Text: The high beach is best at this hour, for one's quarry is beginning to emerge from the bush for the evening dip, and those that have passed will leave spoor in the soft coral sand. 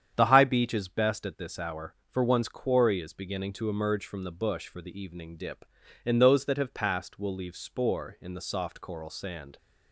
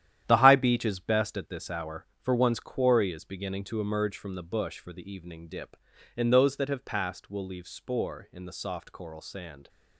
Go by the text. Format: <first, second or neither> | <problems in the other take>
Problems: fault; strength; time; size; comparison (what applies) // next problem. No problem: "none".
first | gets quieter; strong; throughout; 9.5 dB // starts louder than the rest; strong; until 1.2 s; 11 dB; strong in the first